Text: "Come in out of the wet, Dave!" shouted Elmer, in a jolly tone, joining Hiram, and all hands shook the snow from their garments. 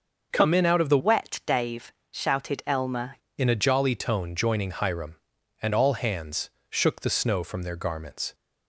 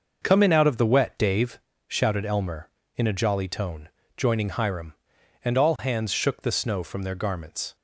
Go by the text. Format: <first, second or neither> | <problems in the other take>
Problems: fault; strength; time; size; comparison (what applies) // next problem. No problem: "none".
second | starts louder than the rest; until 1.3 s; 6 dB // changes voice from "wet" to "Elmer"; from 0.9 to 3.1 s; 2.2 s long // pauses between "hands" and "shook"; slight; at 6.5 s; 0.18 s long